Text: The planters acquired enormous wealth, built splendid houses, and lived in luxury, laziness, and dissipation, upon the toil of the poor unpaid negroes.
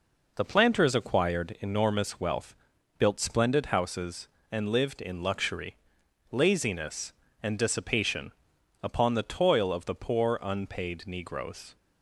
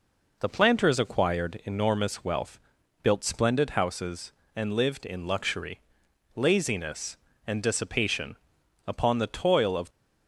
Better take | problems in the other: first | stops before "the poor unpaid negroes"; at 9.8 s

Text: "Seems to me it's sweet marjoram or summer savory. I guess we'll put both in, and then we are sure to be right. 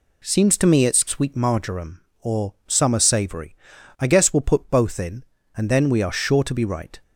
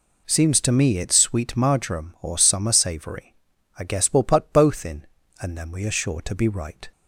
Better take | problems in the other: neither | none

